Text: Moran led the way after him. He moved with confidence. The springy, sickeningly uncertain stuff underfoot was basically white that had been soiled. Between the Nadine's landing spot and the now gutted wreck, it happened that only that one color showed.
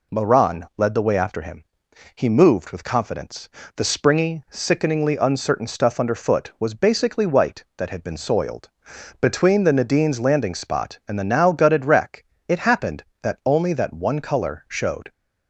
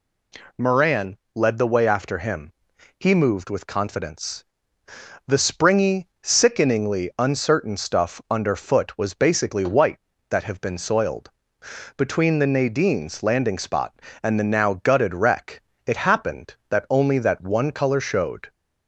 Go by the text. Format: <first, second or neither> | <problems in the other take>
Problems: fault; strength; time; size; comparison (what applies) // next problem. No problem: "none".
first | pauses between "Moran" and "led"; slight; at 1.1 s; 0.18 s long // says "have" for "had"; at 10.4 s